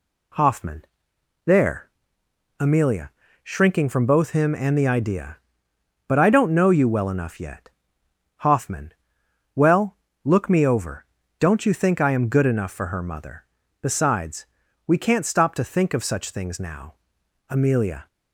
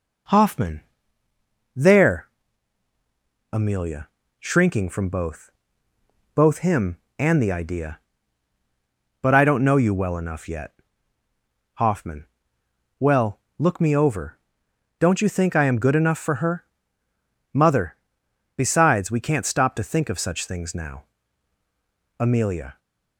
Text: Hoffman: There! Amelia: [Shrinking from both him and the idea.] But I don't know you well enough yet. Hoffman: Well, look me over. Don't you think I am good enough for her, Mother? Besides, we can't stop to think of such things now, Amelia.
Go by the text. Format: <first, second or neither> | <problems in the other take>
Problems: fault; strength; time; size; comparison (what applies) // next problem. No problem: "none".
first | says "both" twice; at 6.3 s